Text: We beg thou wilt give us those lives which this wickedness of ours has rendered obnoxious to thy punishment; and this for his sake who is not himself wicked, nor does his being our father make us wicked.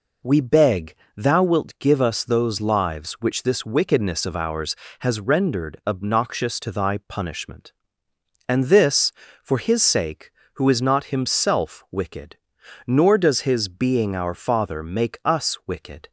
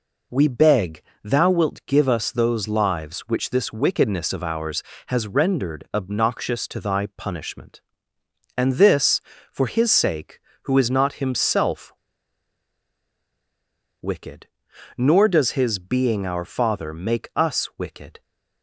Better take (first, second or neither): first